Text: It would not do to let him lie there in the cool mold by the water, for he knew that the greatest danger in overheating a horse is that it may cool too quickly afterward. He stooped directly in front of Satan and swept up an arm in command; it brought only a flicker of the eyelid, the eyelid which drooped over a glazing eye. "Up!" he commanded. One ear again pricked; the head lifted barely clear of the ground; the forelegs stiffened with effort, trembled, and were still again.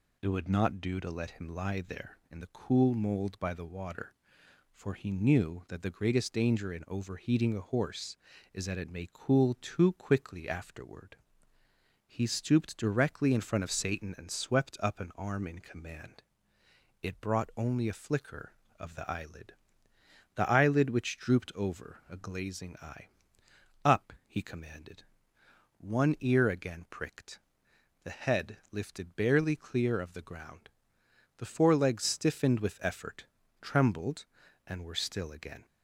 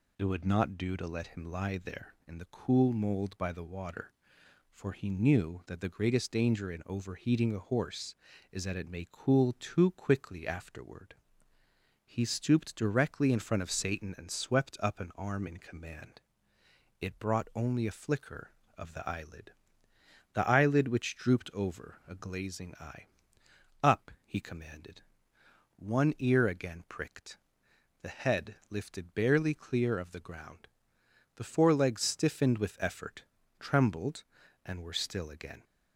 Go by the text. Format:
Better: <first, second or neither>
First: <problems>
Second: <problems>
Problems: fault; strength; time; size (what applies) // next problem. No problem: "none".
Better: neither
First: none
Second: none